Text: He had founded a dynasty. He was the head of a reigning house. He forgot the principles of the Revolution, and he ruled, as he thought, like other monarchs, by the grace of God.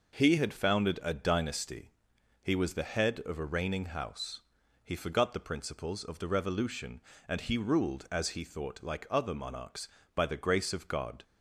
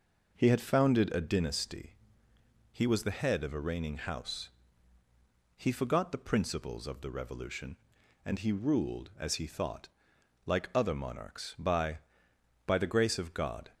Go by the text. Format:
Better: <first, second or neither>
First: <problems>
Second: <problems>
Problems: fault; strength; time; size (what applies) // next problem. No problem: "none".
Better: first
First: none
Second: says "by" twice; at 12.6 s